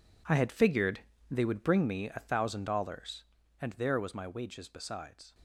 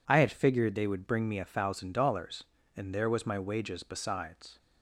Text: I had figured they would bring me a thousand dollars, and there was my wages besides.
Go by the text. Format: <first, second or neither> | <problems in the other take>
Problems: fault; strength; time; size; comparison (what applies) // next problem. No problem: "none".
second | gets quieter; strong; throughout; 14.5 dB // pauses between "figured" and "they"; slight; at 0.9 s; 0.32 s long